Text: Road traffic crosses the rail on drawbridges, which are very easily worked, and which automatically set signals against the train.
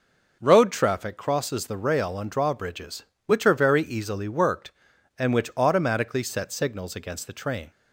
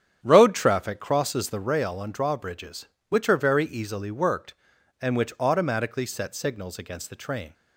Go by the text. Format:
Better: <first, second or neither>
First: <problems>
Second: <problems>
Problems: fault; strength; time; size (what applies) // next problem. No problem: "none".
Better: first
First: none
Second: starts louder than the rest; strong; until 1.8 s; 8.5 dB